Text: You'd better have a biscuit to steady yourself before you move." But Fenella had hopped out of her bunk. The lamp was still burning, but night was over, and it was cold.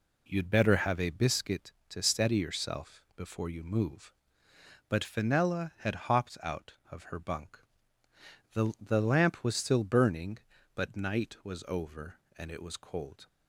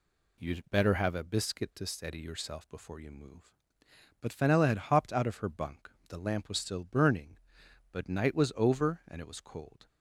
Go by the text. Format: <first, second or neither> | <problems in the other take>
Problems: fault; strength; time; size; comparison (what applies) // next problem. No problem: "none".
second | says "The" twice; at 8.7 s